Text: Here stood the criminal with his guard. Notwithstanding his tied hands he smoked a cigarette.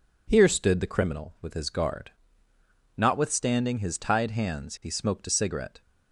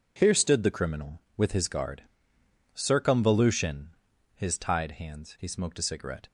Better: first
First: none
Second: says "Circumvolution" for "Notwithstanding"; at 2.7 s

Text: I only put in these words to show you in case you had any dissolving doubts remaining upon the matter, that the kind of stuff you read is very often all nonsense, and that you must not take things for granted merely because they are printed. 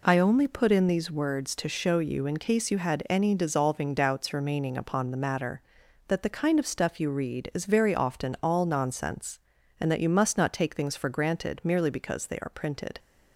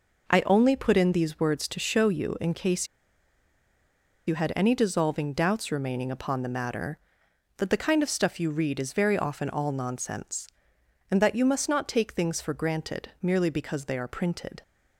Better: first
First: none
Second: pauses between "case" and "you"; strong; at 2.8 s; 1.4 s long

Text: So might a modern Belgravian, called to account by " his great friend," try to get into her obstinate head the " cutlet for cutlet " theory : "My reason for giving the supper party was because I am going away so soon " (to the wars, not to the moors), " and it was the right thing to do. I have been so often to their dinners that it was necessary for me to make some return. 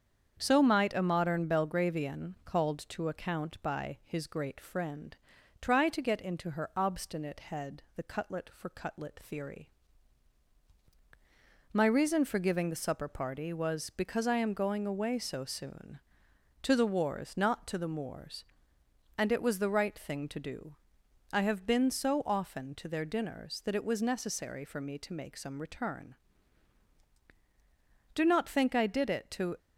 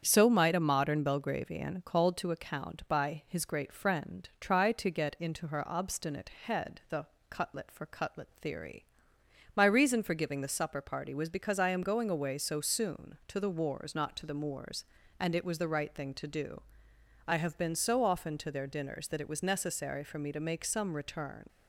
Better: second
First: starts louder than the rest; strong; until 1.3 s; 7.5 dB // goes on to say "Do not think I did it to"; from 28.1 s on; 1.4 s long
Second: starts louder than the rest; strong; until 1.0 s; 8 dB

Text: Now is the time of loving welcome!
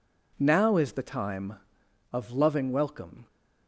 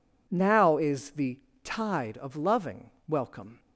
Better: first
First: none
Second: says "tide" for "time"; at 1.6 s // pauses between "loving" and "welcome"; slight; at 2.8 s; 0.18 s long

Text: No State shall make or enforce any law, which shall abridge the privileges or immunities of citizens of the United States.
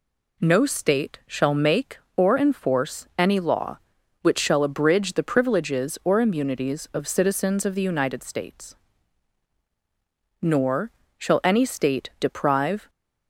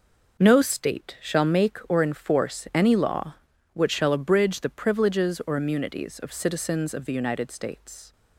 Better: second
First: goes on to say "Nor shall any State deprive"; strong; from 10.4 s on; 2.4 s long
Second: none

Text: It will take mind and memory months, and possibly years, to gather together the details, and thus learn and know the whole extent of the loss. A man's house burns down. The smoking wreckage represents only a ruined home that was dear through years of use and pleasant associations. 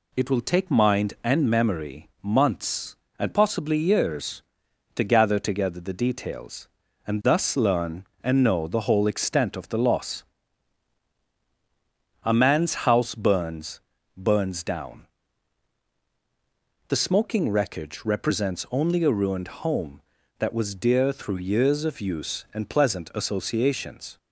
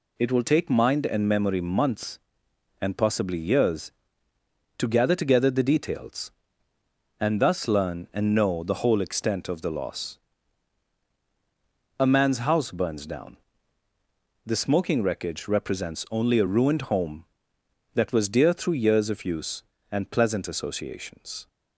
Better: second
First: says "burns" twice; at 14.1 s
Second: none

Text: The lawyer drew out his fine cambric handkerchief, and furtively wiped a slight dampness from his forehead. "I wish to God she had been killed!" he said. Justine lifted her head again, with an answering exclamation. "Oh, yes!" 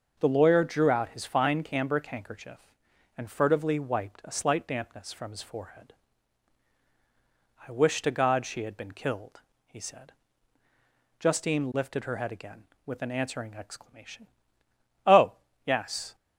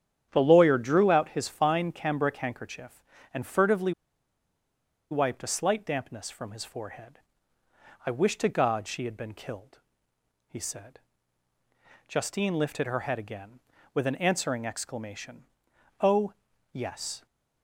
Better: first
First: starts louder than the rest; noticeable; until 1.2 s; 6 dB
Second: starts louder than the rest; strong; until 1.3 s; 9 dB // pauses between "furtively" and "wiped"; at 3.9 s; 1.1 s long

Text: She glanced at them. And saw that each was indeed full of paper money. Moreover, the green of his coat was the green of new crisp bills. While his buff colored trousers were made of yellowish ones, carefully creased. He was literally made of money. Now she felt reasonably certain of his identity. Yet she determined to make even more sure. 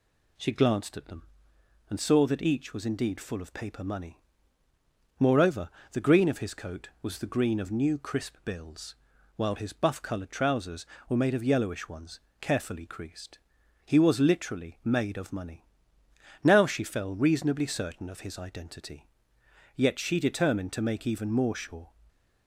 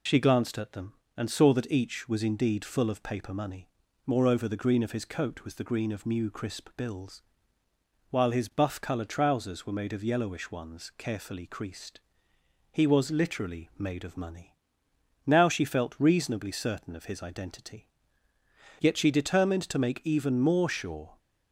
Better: second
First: says "fell" for "felt"; at 16.8 s // stays silent after the last word; slight; from 21.8 s on; 0.6 s long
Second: none

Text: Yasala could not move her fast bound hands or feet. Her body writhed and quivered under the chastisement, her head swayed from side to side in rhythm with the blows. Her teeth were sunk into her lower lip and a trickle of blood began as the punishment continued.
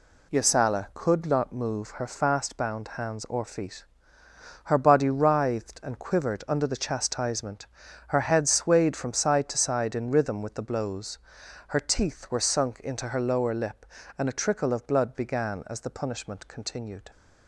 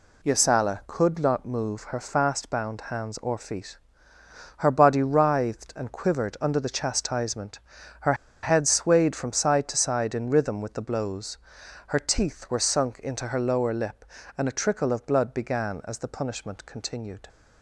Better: first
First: none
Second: pauses between "her" and "head"; slight; at 8.1 s; 0.29 s long

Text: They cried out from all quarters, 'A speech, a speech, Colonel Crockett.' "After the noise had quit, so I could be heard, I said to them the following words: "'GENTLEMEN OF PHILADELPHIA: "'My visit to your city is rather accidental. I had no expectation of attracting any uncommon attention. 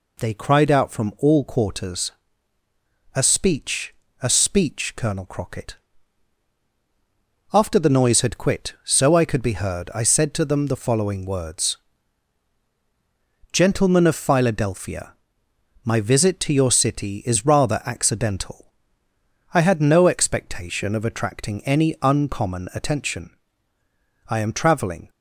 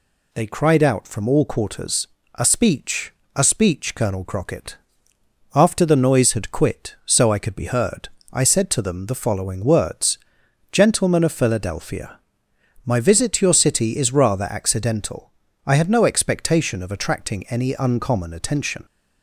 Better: second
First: goes on to say "I am travelling"; noticeable; from 24.2 s on; 0.80 s long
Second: none

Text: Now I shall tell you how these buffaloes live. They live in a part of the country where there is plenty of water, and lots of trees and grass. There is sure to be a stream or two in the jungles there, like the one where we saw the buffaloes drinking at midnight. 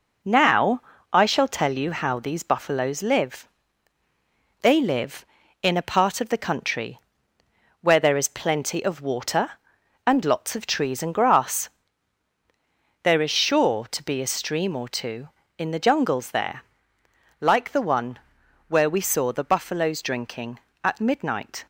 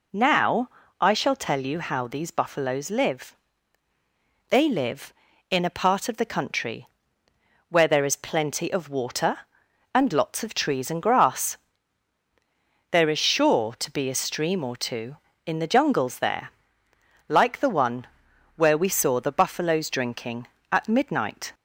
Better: second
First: gets quieter; noticeable; throughout; 4.5 dB // pauses between "Now" and "I"; slight; at 0.8 s; 0.30 s long // pauses between "country" and "where"; noticeable; at 6.9 s; 0.82 s long // pauses between "one" and "where"; noticeable; at 18.1 s; 0.50 s long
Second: pauses between "Now" and "I"; slight; at 0.6 s; 0.30 s long // pauses between "country" and "where"; noticeable; at 6.8 s; 0.82 s long // pauses between "one" and "where"; noticeable; at 18.0 s; 0.50 s long

